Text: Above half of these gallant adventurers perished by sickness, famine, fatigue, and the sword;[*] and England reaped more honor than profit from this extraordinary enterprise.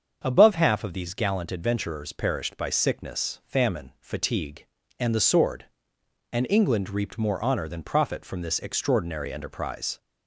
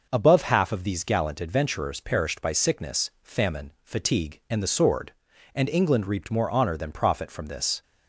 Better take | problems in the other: first | starts louder than the rest; noticeable; until 1.1 s; 6 dB; strong in the first // stops before "extraordinary enterprise"; at 7.8 s

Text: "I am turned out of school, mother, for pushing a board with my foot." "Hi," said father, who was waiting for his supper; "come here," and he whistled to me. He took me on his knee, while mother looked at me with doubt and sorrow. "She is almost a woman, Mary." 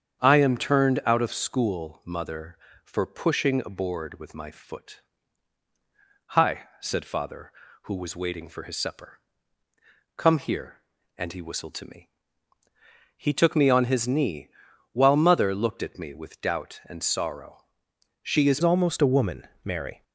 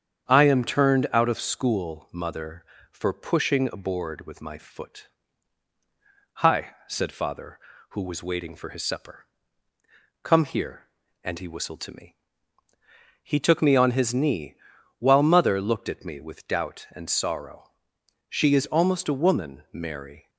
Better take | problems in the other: second | starts louder than the rest; strong; until 1.2 s; 8 dB; strong in the second // changes voice at "almost"; from 18.6 s on; 1.4 s long

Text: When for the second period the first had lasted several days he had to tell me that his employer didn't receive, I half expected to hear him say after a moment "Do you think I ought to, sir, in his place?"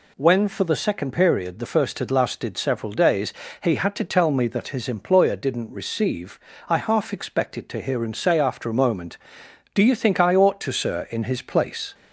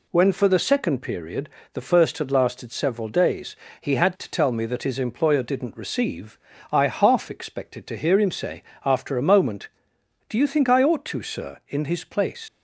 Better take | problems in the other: first | pauses between "period" and "the"; slight; at 1.4 s; 0.24 s long // pauses between "days" and "he"; slight; at 3.5 s; 0.26 s long; slight in the first // pauses between "say" and "after"; slight; at 8.6 s; 0.22 s long // leaves "place" unfinished; at 12.4 s; 105 ms

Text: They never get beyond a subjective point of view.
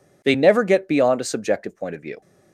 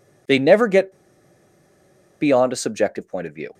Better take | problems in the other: first | pauses between "get" and "beyond"; strong; at 0.9 s; 1.2 s long

